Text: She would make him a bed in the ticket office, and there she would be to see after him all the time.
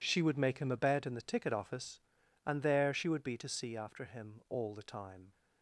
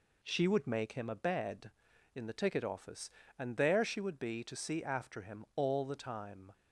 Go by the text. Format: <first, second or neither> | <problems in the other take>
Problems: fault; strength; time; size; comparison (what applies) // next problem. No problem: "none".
neither | none